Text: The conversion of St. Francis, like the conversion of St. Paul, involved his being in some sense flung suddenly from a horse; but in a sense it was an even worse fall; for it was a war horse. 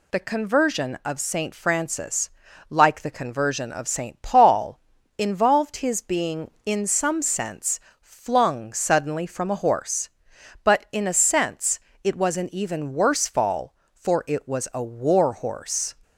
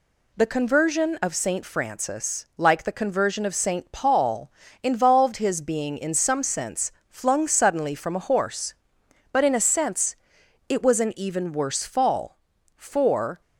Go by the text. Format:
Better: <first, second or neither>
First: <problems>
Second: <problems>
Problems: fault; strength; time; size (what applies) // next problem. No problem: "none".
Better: first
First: pauses between "sense" and "flung"; slight; at 7.8 s; 0.18 s long // pauses between "sense" and "it"; slight; at 11.8 s; 0.24 s long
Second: pauses between "sense" and "flung"; slight; at 6.9 s; 0.20 s long // pauses between "sense" and "it"; noticeable; at 10.1 s; 0.54 s long // stops before "it was a war horse"; at 13.4 s